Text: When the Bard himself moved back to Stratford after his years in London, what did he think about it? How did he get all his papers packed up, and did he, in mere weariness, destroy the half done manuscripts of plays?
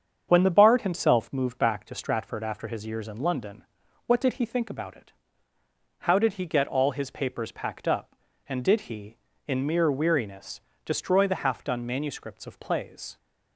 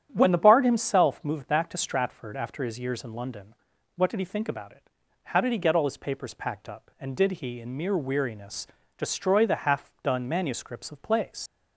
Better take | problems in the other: first | starts louder than the rest; strong; until 1.1 s; 10 dB; strong in the first // leaves "plays" unfinished; at 11.4 s; 75 ms

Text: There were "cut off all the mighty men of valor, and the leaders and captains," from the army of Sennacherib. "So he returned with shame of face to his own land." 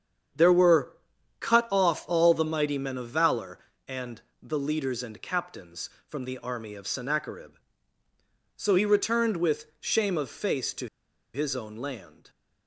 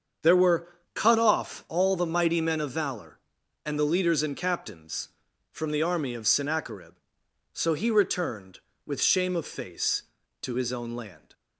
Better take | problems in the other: second | starts louder than the rest; strong; until 1.8 s; 7.5 dB; strong in the second // pauses between "were" and "cut"; at 0.9 s; 0.44 s long; slight in the second // pauses between "and" and "the"; slight; at 4.2 s; 0.18 s long // pauses between "to" and "his"; noticeable; at 10.8 s; 0.47 s long

